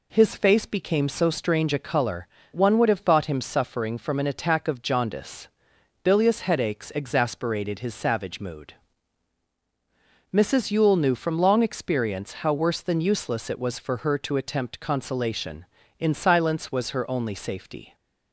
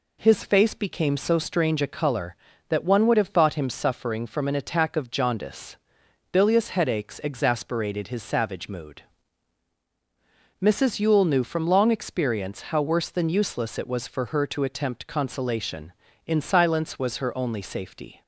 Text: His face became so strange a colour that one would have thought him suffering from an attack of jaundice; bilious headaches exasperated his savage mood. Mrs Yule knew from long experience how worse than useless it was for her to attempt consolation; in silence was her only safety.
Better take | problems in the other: second | skips "that"; at 2.4 s

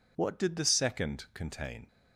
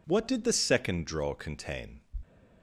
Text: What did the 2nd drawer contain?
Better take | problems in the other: second | skips "drawer"; at 1.2 s

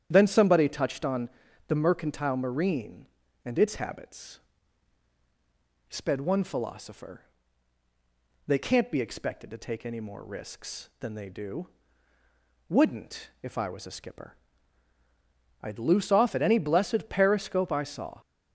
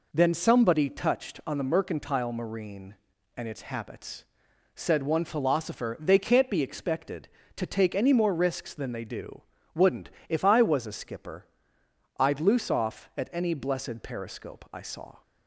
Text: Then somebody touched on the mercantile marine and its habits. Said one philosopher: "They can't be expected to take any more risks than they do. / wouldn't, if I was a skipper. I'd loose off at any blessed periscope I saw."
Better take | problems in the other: second | starts louder than the rest; strong; until 1.1 s; 10 dB // pauses between "on" and "the"; at 1.2 s; 0.40 s long // says "Sped" for "Said"; at 5.8 s

